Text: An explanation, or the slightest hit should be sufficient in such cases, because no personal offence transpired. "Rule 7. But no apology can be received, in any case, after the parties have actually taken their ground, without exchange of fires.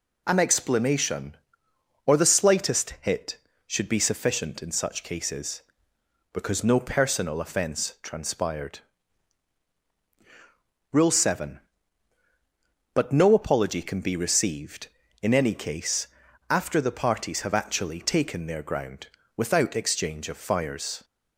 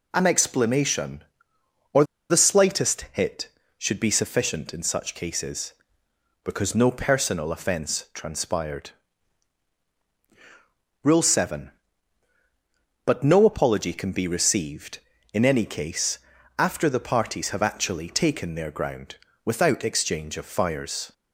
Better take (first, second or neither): first